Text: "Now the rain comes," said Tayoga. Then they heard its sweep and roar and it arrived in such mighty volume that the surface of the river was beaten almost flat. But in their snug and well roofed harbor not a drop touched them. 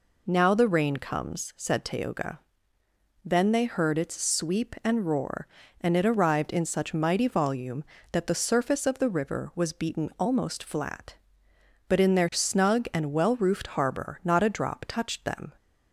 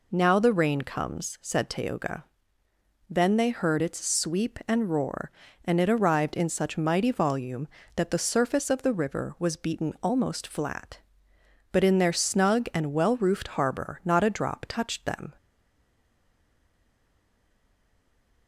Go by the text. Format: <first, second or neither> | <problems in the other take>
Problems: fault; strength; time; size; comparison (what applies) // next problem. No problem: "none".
first | stays silent after the last word; strong; from 15.3 s on; 3.1 s long